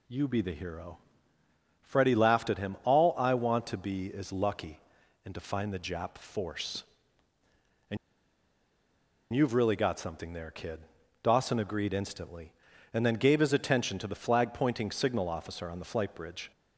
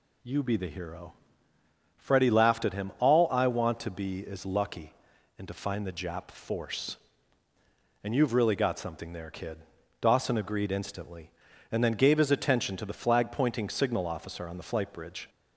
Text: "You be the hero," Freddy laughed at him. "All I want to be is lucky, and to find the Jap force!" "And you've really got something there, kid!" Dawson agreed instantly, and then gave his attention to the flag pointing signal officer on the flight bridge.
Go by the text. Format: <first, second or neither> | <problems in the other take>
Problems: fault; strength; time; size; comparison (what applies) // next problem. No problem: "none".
second | pauses between "And" and "you've"; strong; at 7.9 s; 1.3 s long